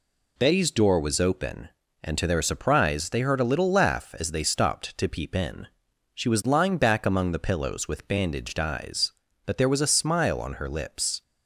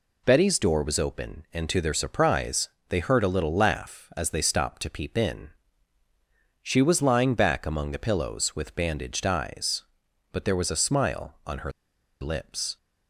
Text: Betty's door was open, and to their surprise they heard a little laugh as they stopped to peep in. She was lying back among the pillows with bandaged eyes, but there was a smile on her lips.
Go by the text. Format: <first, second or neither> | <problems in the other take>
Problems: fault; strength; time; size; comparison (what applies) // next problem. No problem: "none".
first | pauses between "surprise" and "they"; slight; at 2.6 s; 0.20 s long // pauses between "her" and "lips"; noticeable; at 11.7 s; 0.51 s long